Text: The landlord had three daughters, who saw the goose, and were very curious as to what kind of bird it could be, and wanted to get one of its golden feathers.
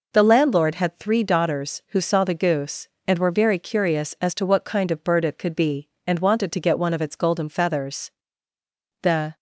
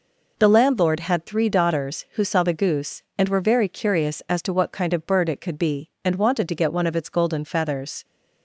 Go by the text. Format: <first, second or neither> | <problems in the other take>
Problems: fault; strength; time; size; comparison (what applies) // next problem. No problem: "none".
second | goes on to say "The"; slight; from 9.0 s on; 0.34 s long